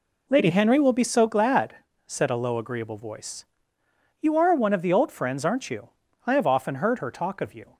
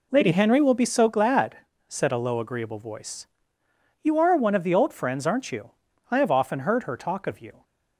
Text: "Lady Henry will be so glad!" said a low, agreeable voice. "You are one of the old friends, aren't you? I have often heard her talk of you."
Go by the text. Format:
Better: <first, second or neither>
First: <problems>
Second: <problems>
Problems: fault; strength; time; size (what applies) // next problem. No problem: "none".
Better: neither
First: none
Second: none